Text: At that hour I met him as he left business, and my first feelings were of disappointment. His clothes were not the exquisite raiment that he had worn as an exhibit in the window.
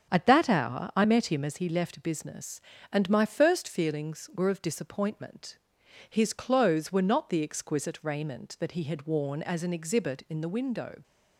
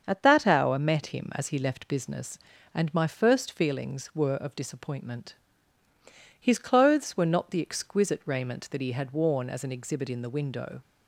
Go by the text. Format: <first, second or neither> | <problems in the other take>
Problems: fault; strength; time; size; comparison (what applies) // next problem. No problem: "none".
first | starts louder than the rest; until 1.0 s; 7 dB; strong in the first // skips "I"; at 0.8 s